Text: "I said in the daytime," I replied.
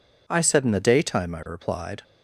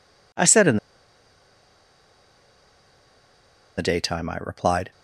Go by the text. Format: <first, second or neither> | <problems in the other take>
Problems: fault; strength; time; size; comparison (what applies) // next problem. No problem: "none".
first | pauses between "in" and "the"; strong; at 0.7 s; 2.9 s long